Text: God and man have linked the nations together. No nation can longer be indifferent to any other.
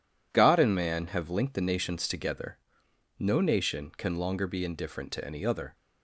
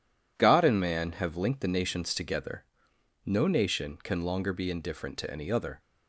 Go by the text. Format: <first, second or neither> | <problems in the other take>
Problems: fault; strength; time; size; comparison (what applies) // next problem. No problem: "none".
neither | none